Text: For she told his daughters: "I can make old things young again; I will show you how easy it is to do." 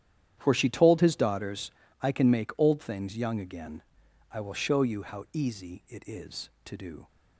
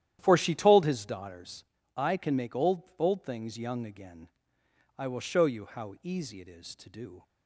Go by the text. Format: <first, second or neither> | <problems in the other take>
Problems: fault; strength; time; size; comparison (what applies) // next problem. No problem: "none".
first | starts louder than the rest; strong; until 1.2 s; 11 dB; strong in the first // says "old" twice; at 2.9 s